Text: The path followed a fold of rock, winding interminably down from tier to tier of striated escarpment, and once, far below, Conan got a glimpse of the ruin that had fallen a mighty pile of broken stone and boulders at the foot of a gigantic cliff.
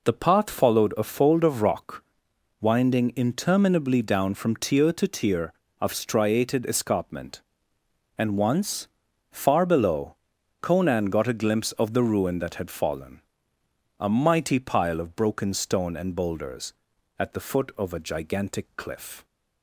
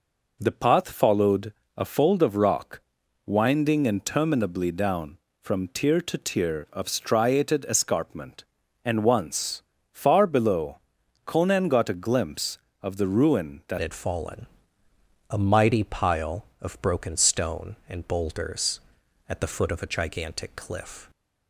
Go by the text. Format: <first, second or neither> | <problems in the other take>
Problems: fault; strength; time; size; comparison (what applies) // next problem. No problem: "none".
first | pauses between "followed" and "a"; slight; at 1.5 s; 0.24 s long // changes voice at "had"; from 13.7 s on; 7.3 s long // pauses between "fallen" and "a"; noticeable; at 14.4 s; 0.82 s long; noticeable in the first